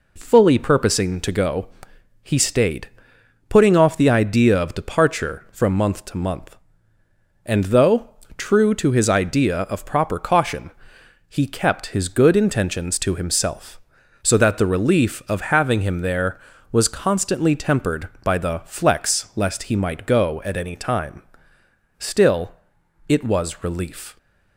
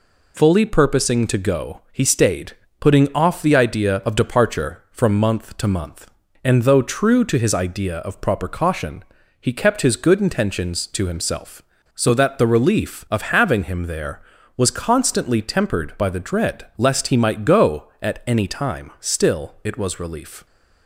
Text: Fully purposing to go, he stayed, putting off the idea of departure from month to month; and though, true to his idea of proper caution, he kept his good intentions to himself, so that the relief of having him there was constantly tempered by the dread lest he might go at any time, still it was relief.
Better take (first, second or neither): second